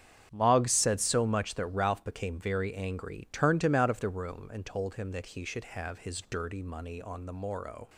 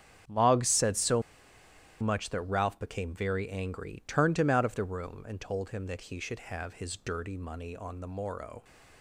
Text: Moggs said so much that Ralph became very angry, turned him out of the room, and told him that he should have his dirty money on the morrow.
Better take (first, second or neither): first